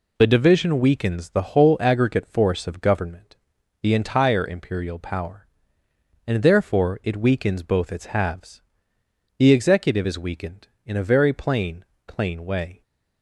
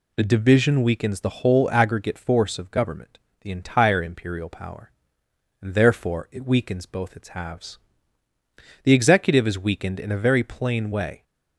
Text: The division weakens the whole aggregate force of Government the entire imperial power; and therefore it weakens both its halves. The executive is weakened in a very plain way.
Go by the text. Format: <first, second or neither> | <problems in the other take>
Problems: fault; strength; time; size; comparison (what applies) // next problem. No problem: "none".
second | pauses between "Government" and "the"; noticeable; at 3.3 s; 0.46 s long; slight in the second // says "plain" twice; at 12.0 s